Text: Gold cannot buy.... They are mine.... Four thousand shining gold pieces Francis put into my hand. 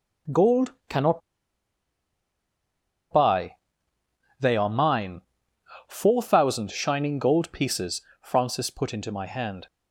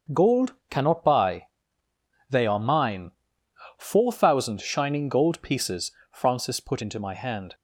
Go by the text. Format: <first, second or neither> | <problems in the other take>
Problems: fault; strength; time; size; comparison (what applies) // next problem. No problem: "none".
second | starts louder than the rest; until 3.4 s; 6.5 dB; also in the second // pauses between "Gold" and "cannot"; slight; at 0.7 s; 0.16 s long; slight in the second // pauses between "cannot" and "buy"; strong; at 1.2 s; 1.9 s long // pauses between "pieces" and "Francis"; slight; at 8.0 s; 0.22 s long; slight in the second